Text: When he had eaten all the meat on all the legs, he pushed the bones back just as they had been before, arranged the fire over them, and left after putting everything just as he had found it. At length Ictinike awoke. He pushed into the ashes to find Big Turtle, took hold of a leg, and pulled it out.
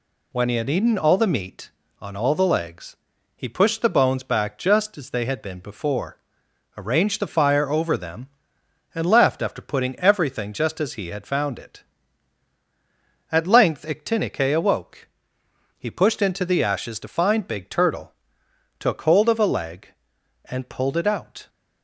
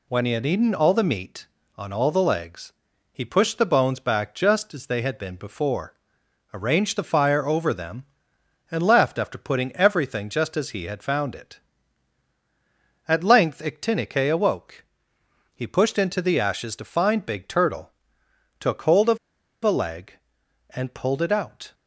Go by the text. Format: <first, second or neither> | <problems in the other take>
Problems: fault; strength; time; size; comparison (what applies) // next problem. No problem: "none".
first | pauses between "of" and "a"; at 19.1 s; 0.45 s long